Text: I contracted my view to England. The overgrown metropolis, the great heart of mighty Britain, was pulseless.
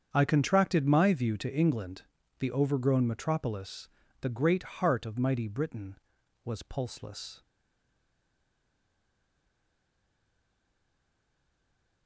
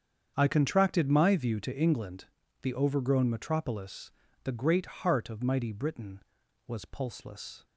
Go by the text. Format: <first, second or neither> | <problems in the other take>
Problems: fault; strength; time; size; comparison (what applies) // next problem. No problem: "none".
second | starts louder than the rest; strong; until 1.1 s; 8 dB; strong in the second // stays silent after the last word; strong; from 7.4 s on; 4.6 s long